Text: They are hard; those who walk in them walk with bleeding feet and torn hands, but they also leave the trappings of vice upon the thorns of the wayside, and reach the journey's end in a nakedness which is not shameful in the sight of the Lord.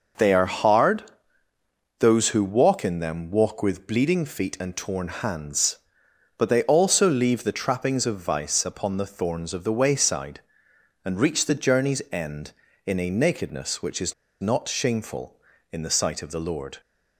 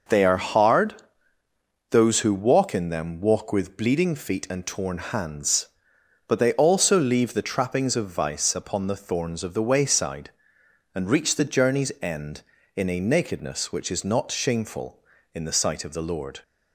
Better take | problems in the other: second | starts louder than the rest; until 2.1 s; 6.5 dB; also in the second // pauses between "is" and "not"; slight; at 14.1 s; 0.27 s long

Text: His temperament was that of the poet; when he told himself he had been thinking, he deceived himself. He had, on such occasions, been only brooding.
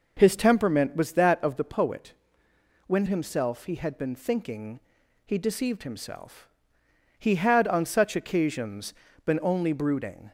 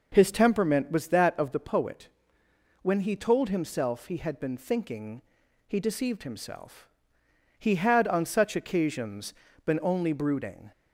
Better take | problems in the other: second | skips "he told"; at 3.0 s

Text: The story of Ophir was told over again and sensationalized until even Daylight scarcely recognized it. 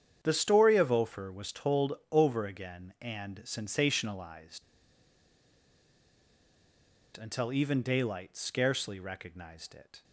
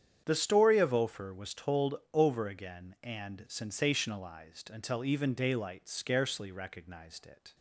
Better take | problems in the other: second | starts louder than the rest; strong; until 1.2 s; 8.5 dB; strong in the second // pauses between "told" and "over"; slight; at 1.9 s; 0.18 s long; slight in the second // pauses between "sensationalized" and "until"; strong; at 4.6 s; 2.5 s long

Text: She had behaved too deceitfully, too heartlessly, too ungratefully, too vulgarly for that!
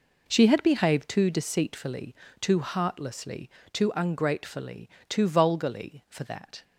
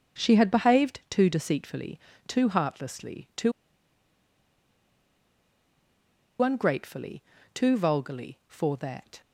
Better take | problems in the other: first | starts louder than the rest; until 1.2 s; 7 dB // pauses between "too" and "ungratefully"; strong; at 3.5 s; 2.9 s long

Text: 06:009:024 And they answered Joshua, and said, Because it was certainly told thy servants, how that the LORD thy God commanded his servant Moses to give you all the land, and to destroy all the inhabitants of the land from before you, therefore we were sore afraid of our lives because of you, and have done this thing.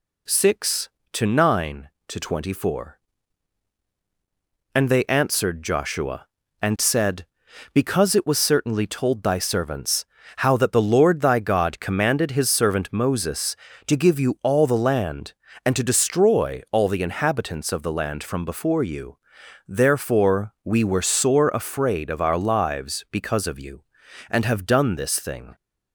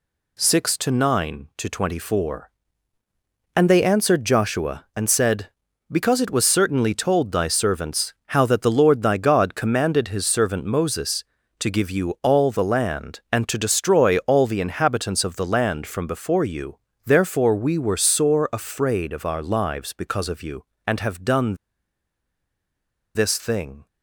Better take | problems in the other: first | pauses between "done" and "this"; strong; at 21.5 s; 1.5 s long

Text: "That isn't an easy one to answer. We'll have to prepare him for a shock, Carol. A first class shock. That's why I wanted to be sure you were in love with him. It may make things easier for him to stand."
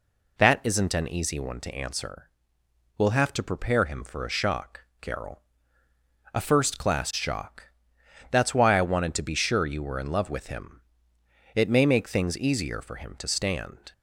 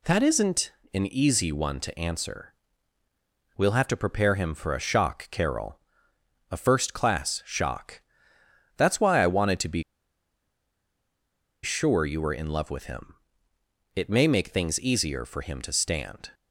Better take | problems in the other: first | pauses between "isn't" and "an"; slight; at 0.7 s; 0.22 s long // pauses between "be" and "sure"; strong; at 9.8 s; 1.8 s long

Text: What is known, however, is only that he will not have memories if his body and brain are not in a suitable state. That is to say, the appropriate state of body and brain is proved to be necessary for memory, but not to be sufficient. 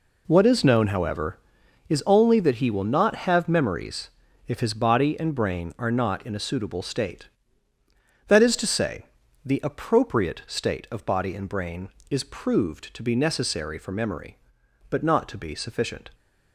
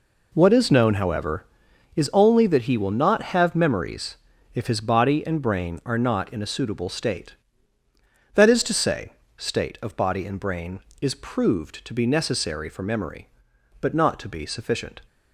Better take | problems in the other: first | pauses between "memories" and "if"; at 4.1 s; 0.38 s long; also in the first // skips "the appropriate"; at 9.2 s

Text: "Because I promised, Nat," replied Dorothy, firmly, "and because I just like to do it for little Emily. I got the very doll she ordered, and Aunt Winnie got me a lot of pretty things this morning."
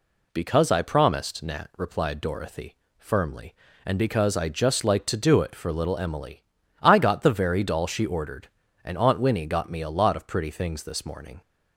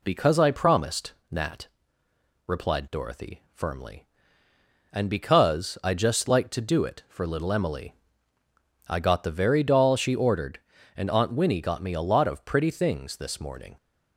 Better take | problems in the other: neither | none

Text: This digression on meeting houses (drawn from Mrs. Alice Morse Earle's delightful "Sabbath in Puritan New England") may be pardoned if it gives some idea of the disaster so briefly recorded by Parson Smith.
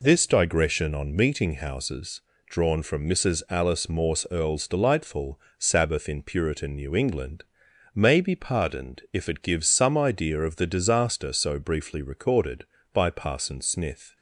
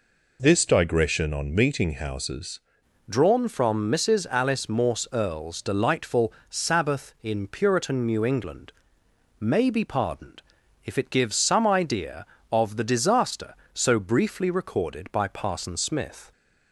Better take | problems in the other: first | changes voice at "drawn"; from 3.0 s on; 13.3 s long // pauses between "delightful" and "Sabbath"; slight; at 6.3 s; 0.16 s long; slight in the first // pauses between "pardoned" and "if"; at 10.4 s; 0.42 s long

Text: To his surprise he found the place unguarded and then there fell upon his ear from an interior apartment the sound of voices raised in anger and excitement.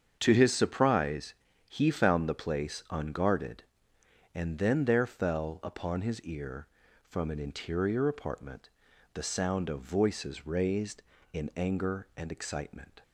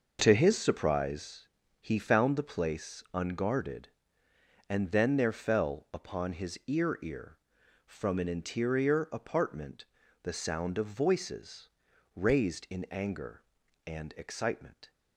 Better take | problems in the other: first | starts louder than the rest; noticeable; until 1.2 s; 6 dB; strong in the first // pauses between "surprise" and "he"; slight; at 1.4 s; 0.32 s long; slight in the first // says "ear" twice; at 7.0 s // pauses between "apartment" and "the"; at 9.8 s; 0.38 s long; noticeable in the first // pauses between "voices" and "raised"; at 11.7 s; 0.44 s long

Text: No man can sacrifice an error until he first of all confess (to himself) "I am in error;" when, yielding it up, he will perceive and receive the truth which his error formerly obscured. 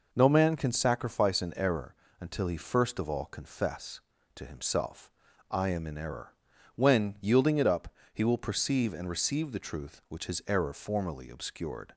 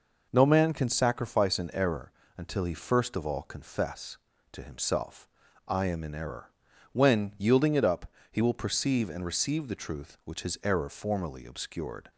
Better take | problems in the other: neither | pauses between "error" and "until"; slight; the same in both

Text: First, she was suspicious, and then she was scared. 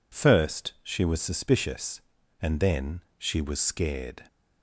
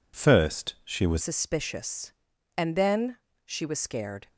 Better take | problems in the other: first | changes voice at "suspicious"; from 1.2 s on; 3.0 s long // pauses between "then" and "she"; slight; at 3.1 s; 0.28 s long; slight in the first

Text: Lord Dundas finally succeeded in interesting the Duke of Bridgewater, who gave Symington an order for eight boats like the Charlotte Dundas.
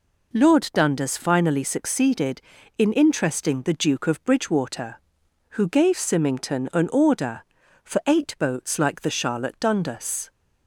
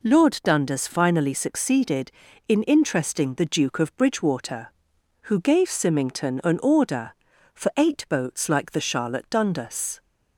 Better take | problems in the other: neither | none

